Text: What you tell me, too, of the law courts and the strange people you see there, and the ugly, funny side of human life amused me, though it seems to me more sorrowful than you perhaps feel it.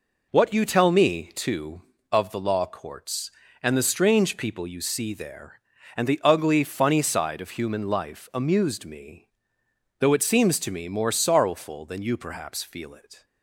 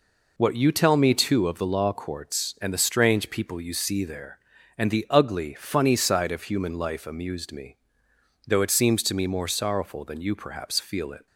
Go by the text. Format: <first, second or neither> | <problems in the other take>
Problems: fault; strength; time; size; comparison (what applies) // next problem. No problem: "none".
neither | none